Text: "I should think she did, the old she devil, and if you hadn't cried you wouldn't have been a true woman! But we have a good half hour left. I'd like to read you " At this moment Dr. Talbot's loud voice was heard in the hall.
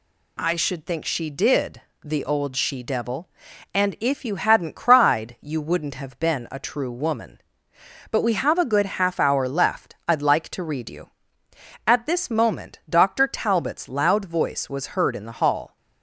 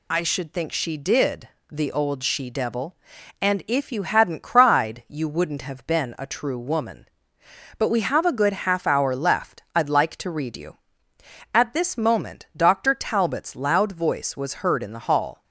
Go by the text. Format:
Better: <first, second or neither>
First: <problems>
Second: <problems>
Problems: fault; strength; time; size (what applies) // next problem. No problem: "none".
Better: first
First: none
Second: loses the start of "I"; at 0.1 s; 60 ms